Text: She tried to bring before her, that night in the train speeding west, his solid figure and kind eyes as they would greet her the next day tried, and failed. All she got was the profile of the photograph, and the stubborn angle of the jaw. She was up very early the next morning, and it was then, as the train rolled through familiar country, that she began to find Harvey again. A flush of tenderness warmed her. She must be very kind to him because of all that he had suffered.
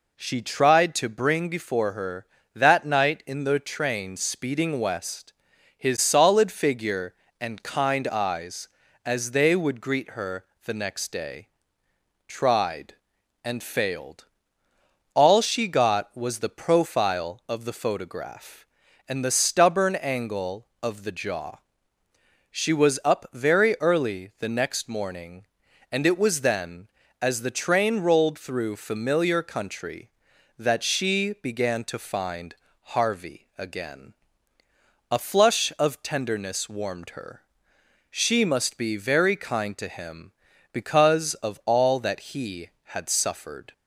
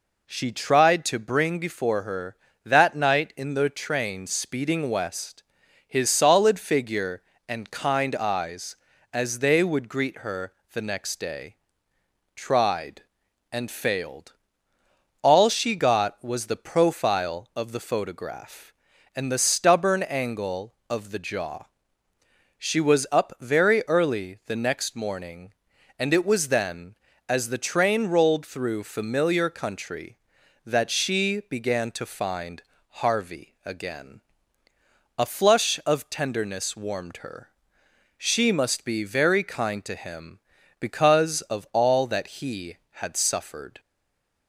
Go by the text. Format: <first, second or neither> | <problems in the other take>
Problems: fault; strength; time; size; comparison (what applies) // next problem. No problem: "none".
first | pauses between "her" and "the"; slight; at 10.5 s; 0.20 s long; slight in the first // pauses between "day" and "tried"; noticeable; at 11.5 s; 0.80 s long; noticeable in the first // pauses between "find" and "Harvey"; slight; at 32.6 s; 0.26 s long; slight in the first // stays silent after the last word; slight; from 43.7 s on; 0.7 s long